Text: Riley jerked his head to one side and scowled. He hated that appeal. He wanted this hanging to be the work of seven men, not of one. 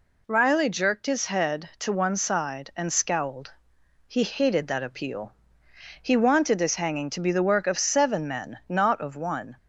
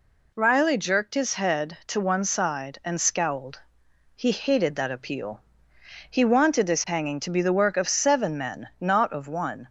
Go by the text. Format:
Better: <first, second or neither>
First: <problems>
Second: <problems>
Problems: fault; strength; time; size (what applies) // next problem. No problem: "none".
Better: neither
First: none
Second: none